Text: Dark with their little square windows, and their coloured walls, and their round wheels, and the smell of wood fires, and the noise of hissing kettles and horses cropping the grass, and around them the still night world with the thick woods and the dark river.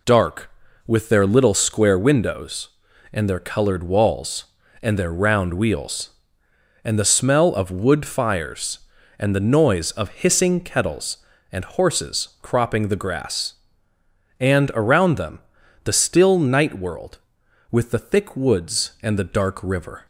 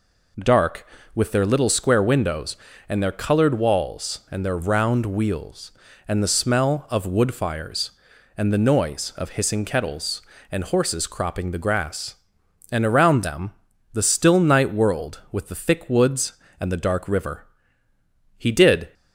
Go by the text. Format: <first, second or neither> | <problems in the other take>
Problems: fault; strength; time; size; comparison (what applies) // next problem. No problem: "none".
first | pauses between "them" and "the"; at 13.5 s; 0.38 s long; noticeable in the first // goes on to say "He did"; from 18.3 s on; 0.56 s long